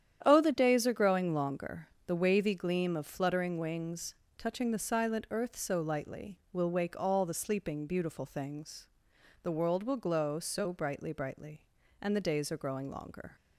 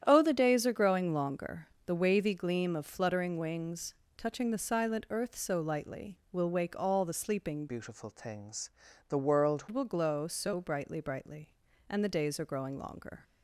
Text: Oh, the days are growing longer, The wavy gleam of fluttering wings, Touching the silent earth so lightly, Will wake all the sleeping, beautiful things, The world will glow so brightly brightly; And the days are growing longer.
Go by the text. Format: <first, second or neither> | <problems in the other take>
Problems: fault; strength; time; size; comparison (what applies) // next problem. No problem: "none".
first | starts louder than the rest; strong; until 1.0 s; 10 dB; strong in the first // changes voice from "beautiful" to "world"; from 7.6 to 9.6 s; 2.0 s long